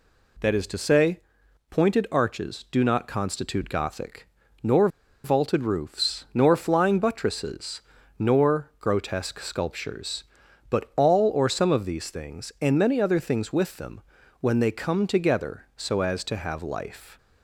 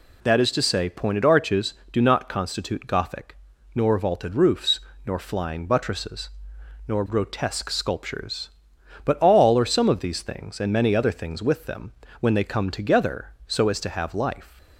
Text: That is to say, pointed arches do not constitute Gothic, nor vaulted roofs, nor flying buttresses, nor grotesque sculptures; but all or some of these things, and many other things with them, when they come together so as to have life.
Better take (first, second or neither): second